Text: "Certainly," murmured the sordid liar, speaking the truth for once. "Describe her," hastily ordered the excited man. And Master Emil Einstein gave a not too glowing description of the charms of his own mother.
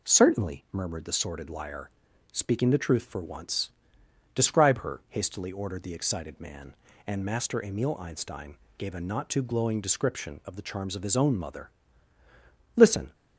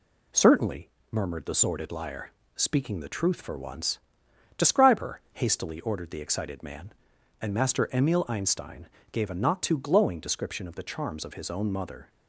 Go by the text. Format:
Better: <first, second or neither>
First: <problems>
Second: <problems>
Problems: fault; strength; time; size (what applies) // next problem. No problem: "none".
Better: second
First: pauses between "Einstein" and "gave"; slight; at 8.5 s; 0.20 s long // goes on to say "Listen"; slight; from 12.7 s on; 0.38 s long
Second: pauses between "Einstein" and "gave"; slight; at 8.8 s; 0.26 s long